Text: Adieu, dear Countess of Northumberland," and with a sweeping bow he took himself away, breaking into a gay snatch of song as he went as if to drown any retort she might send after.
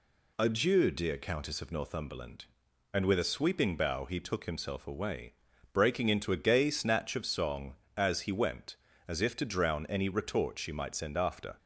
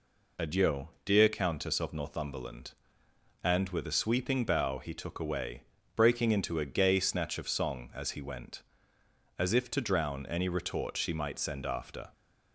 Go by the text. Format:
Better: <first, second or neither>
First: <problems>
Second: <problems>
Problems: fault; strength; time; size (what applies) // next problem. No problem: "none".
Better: first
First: none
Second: skips "himself"; at 5.1 s